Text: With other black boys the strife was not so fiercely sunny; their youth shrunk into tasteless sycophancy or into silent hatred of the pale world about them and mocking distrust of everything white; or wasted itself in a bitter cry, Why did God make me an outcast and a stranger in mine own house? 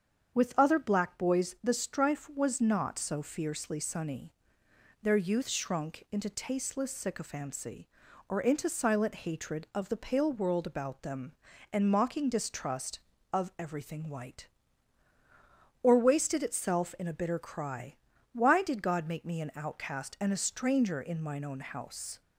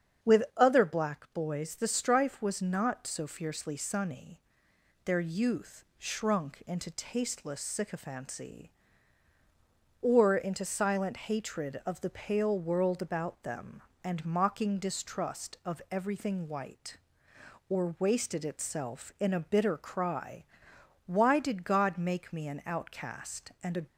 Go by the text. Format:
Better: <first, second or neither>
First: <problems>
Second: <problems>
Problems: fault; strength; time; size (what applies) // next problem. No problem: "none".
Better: first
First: starts louder than the rest; strong; until 1.3 s; 7.5 dB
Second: starts louder than the rest; strong; until 1.4 s; 8 dB // stops before "stranger in mine own house"; at 23.8 s